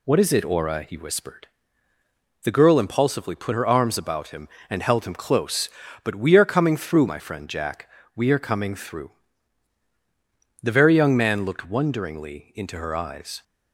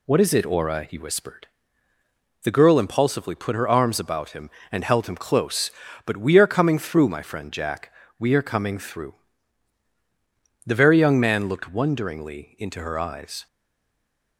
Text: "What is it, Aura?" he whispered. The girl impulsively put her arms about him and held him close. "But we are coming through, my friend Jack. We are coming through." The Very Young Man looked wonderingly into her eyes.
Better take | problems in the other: first | stays silent after the last word; slight; from 13.4 s on; 0.9 s long

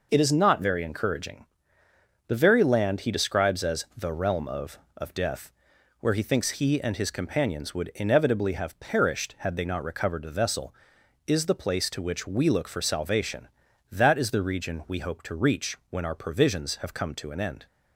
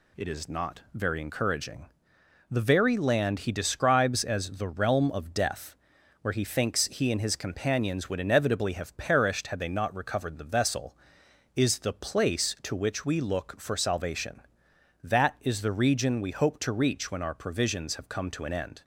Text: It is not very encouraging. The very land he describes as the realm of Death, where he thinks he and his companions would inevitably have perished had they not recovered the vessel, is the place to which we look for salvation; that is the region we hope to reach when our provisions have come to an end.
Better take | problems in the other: second | says "of" twice; at 4.9 s

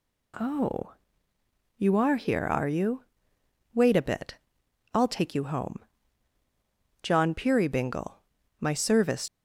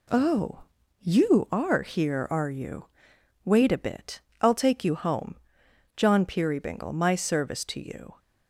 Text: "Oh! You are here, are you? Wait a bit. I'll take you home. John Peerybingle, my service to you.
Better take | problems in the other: second | stops before "to you"; at 9.2 s

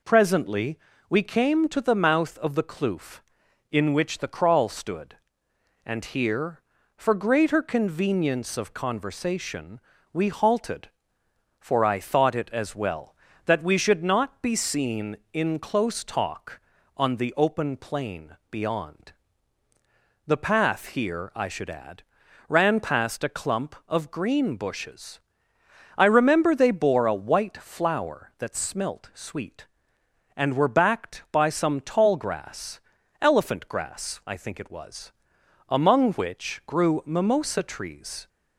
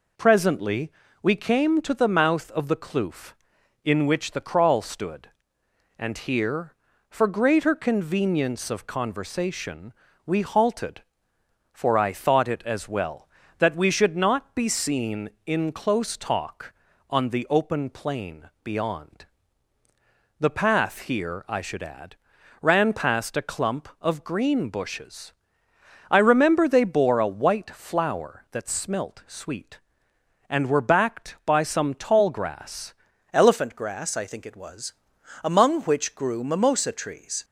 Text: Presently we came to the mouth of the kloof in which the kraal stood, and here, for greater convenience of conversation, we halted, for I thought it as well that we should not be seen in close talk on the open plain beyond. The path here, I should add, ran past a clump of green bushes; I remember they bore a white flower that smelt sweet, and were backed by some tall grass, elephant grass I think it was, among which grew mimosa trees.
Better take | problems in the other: first | pauses between "Presently" and "we"; slight; at 0.9 s; 0.30 s long; slight in the first // pauses between "plain" and "beyond"; slight; at 18.4 s; 0.16 s long; slight in the first // changes voice at "elephant"; from 33.3 s on; 4.1 s long

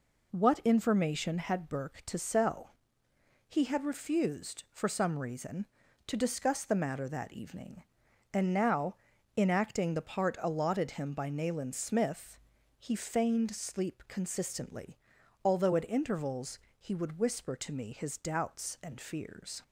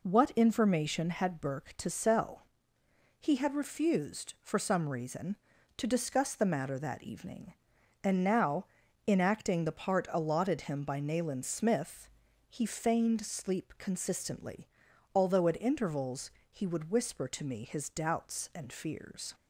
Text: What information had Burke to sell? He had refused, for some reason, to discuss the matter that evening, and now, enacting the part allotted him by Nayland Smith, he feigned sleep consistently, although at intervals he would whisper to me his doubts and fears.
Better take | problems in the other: neither | pauses between "intervals" and "he"; slight; the same in both

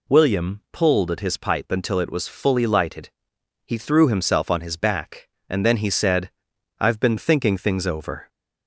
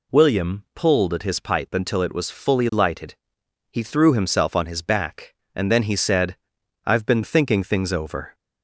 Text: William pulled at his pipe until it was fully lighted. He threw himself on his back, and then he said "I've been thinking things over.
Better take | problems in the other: neither | pauses between "said" and "I've"; noticeable; the same in both

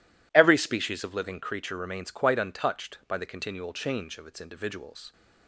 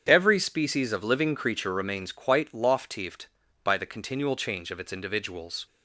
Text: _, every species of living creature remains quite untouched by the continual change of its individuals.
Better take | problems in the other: first | starts louder than the rest; strong; until 1.0 s; 8 dB // says "loftieft" for "untouched"; at 2.5 s

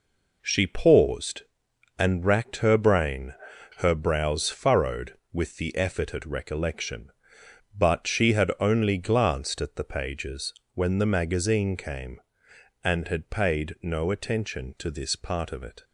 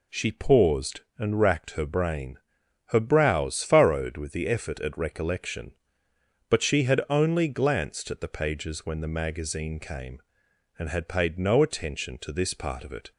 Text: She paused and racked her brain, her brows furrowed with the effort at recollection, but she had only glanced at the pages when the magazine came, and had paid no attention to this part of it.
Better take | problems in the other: second | gets quieter; strong; throughout; 7.5 dB // pauses between "pages" and "when"; slight; at 10.5 s; 0.20 s long

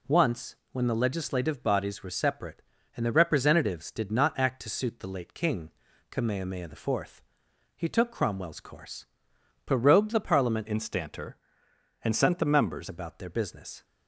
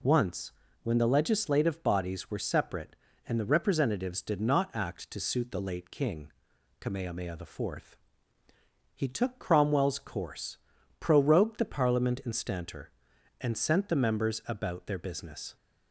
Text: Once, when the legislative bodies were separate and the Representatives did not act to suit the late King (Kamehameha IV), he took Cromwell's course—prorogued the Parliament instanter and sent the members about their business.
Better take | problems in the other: second | changes voice from "instanter" to "members"; from 10.6 to 12.8 s; 2.2 s long

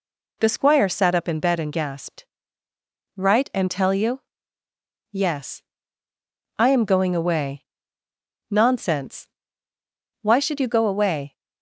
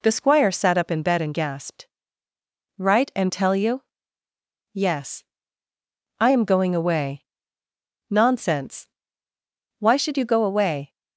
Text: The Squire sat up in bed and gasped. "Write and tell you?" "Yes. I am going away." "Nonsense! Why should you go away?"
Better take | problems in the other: neither | none

